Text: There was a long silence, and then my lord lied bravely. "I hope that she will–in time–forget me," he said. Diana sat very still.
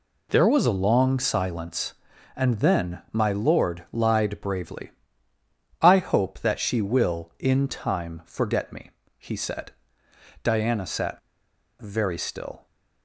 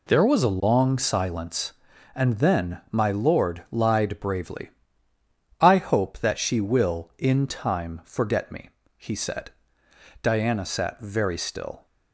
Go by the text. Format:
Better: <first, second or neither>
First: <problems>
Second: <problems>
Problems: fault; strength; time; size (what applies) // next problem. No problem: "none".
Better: second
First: pauses between "sat" and "very"; noticeable; at 11.1 s; 0.59 s long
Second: none